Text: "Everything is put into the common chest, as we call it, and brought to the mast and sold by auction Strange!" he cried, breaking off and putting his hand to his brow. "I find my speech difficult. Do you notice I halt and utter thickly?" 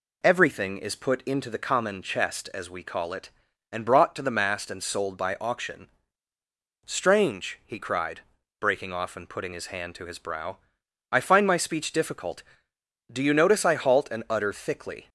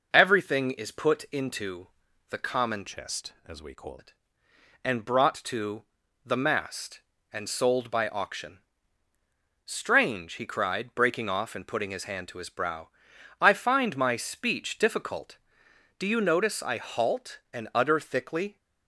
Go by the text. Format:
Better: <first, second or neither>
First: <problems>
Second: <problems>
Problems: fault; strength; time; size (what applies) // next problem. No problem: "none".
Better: first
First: pauses between "auction" and "Strange"; noticeable; at 5.8 s; 0.94 s long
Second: pauses between "into" and "the"; at 1.8 s; 0.42 s long // changes voice from "chest" to "call"; from 2.8 to 3.9 s; 1.1 s long // pauses between "to" and "the"; at 5.8 s; 0.42 s long // pauses between "auction" and "Strange"; at 8.5 s; 1.0 s long